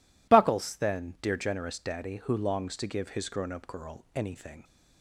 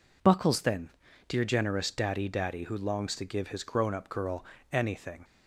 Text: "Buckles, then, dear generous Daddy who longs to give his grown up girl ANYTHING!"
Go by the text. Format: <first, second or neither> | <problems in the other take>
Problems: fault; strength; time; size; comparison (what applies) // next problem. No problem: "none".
first | says "Daddy" twice; at 2.2 s // pauses between "girl" and "ANYTHING"; slight; at 4.4 s; 0.26 s long